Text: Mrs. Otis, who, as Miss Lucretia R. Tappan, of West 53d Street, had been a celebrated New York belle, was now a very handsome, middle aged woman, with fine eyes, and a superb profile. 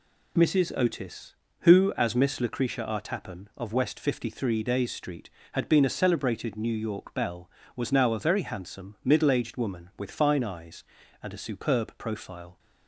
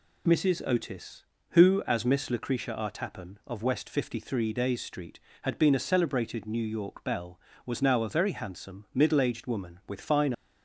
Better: first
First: none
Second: stops before "eyes and a superb profile"; at 10.3 s

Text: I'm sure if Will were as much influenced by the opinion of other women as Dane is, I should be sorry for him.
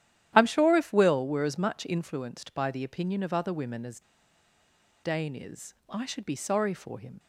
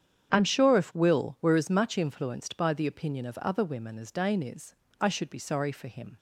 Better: second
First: starts louder than the rest; strong; until 1.3 s; 11.5 dB // pauses between "as" and "Dane"; at 3.9 s; 1.0 s long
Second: starts louder than the rest; strong; until 1.3 s; 8.5 dB

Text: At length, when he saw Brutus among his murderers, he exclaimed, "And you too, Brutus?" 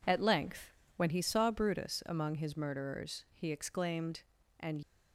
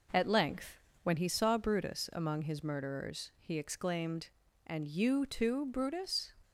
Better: second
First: stops before "you too Brutus"; at 4.8 s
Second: none

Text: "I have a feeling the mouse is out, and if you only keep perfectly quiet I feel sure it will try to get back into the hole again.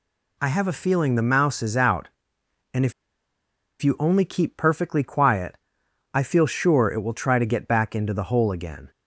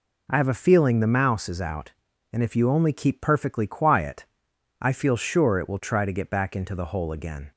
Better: second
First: pauses between "if" and "you"; noticeable; at 2.9 s; 0.89 s long // pauses between "quiet" and "I"; noticeable; at 5.5 s; 0.56 s long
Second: pauses between "quiet" and "I"; noticeable; at 4.2 s; 0.56 s long

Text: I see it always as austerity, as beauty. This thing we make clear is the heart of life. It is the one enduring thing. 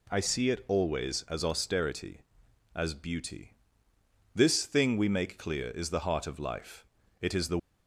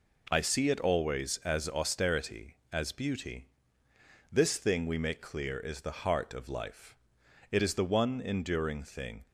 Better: second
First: stops before "one enduring thing"; at 7.5 s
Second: none

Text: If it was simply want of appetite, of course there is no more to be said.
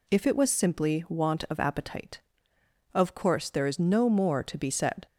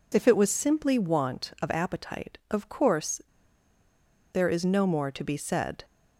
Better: first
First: none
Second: pauses between "course" and "there"; at 3.1 s; 1.1 s long

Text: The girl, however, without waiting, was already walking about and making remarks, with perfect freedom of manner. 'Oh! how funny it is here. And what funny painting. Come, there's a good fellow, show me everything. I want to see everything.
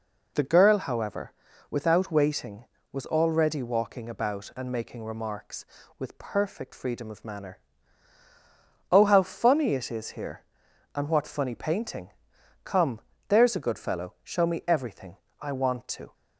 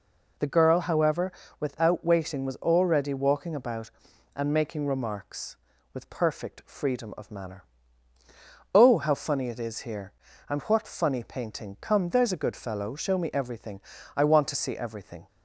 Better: second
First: stops before "see everything"; at 16.1 s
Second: none

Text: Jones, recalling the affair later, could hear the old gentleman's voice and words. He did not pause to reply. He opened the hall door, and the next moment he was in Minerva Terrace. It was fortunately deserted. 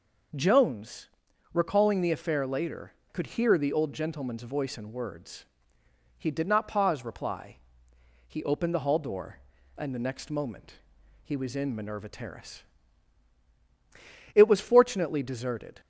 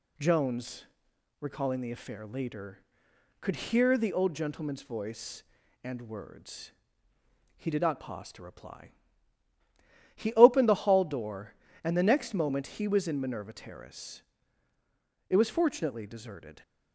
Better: second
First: skips "to"; at 7.0 s // pauses between "moment" and "he"; noticeable; at 10.7 s; 0.50 s long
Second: none

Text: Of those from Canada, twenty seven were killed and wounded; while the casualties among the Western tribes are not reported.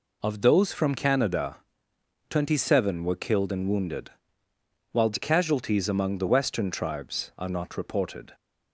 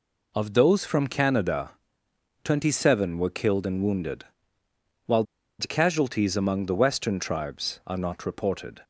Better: first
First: none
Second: pauses between "while" and "the"; at 5.2 s; 0.36 s long

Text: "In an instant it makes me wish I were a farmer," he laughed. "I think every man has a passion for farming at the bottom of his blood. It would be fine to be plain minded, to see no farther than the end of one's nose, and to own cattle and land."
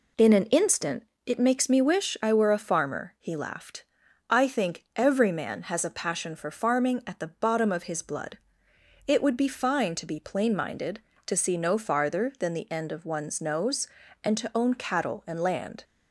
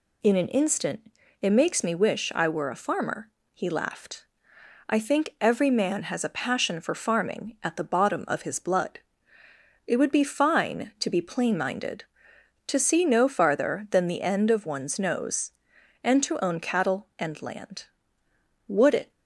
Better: first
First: pauses between "instant" and "it"; slight; at 1.0 s; 0.22 s long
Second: pauses between "instant" and "it"; slight; at 1.1 s; 0.30 s long // goes on to say "Would it"; slight; from 18.6 s on; 0.44 s long

